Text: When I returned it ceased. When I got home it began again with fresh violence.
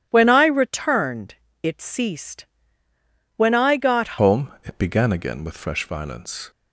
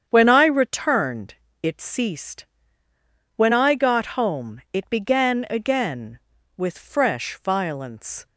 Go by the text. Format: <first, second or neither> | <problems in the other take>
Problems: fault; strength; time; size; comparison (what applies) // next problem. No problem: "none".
second | starts louder than the rest; strong; until 1.1 s; 11.5 dB; strong in the second // pauses between "returned" and "it"; slight; at 1.3 s; 0.28 s long; slight in the second // changes voice at "home"; from 4.2 s on; 2.3 s long